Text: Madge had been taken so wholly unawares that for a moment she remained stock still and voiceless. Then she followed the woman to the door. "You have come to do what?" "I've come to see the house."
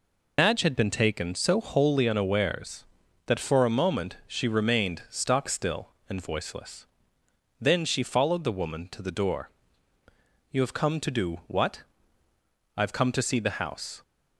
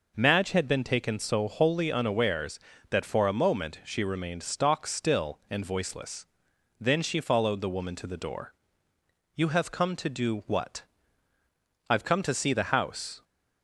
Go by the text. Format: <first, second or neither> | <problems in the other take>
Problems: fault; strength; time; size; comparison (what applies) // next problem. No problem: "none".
second | loses the start of "Madge"; at 0.3 s; 95 ms